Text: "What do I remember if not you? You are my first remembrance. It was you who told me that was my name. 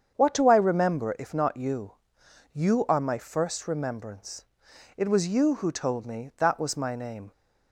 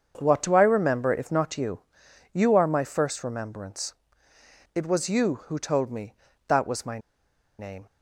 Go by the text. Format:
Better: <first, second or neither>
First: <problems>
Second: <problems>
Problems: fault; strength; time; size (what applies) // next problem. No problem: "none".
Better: first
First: starts louder than the rest; strong; until 1.1 s; 7.5 dB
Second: starts louder than the rest; until 1.1 s; 6.5 dB // pauses between "my" and "name"; noticeable; at 6.9 s; 0.60 s long